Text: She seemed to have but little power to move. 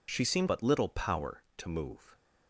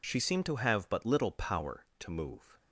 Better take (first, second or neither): second